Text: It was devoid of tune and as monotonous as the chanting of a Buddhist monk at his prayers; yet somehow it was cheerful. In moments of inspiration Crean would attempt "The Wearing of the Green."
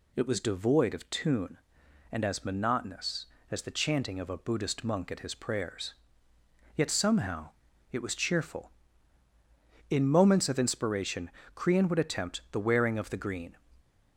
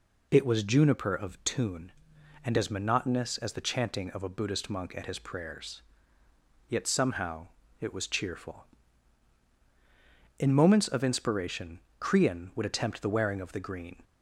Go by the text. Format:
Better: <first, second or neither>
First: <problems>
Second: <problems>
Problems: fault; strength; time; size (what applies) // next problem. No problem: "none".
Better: first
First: pauses between "somehow" and "it"; at 7.4 s; 0.42 s long // pauses between "inspiration" and "Crean"; slight; at 11.3 s; 0.24 s long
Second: says "juniper" for "devoid"; at 0.6 s // pauses between "somehow" and "it"; slight; at 7.4 s; 0.34 s long // pauses between "inspiration" and "Crean"; slight; at 11.8 s; 0.18 s long